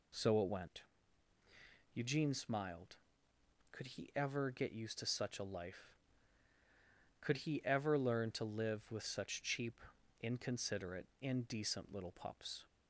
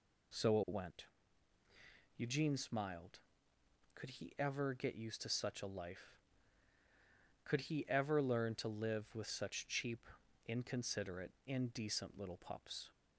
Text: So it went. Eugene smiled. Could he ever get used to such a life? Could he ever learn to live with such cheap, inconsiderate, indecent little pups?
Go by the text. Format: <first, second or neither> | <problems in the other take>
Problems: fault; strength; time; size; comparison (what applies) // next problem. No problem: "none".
neither | none